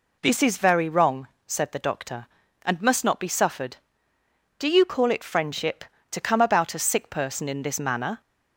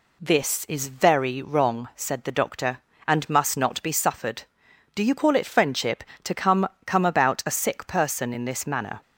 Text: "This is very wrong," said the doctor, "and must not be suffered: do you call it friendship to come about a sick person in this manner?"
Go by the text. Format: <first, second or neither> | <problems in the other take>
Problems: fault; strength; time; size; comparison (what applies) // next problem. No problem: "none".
first | says "come" twice; at 6.8 s